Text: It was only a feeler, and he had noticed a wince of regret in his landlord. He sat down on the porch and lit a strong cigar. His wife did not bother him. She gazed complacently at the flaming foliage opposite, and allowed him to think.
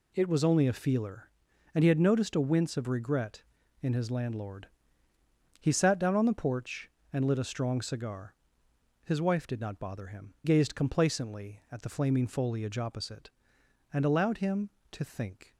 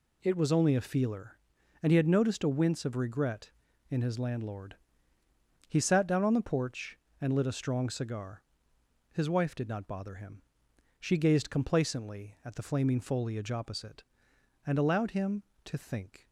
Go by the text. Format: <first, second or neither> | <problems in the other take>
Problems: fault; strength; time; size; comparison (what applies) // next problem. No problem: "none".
second | skips "She"; at 10.3 s